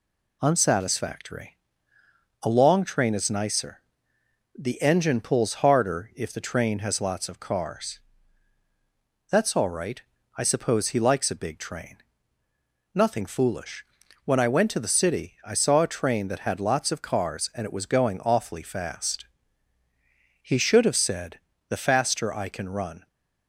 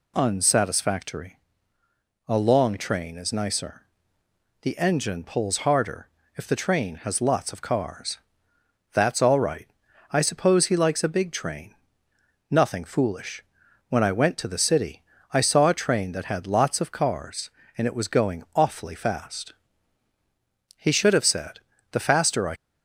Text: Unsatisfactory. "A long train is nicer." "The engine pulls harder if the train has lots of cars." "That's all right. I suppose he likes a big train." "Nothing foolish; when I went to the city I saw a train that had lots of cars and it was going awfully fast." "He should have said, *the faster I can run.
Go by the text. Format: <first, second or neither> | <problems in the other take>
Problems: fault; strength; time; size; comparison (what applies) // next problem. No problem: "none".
first | pauses between "harder" and "if"; slight; at 6.0 s; 0.28 s long // pauses between "city" and "I"; slight; at 15.0 s; 0.30 s long // stops before "can run"; at 22.5 s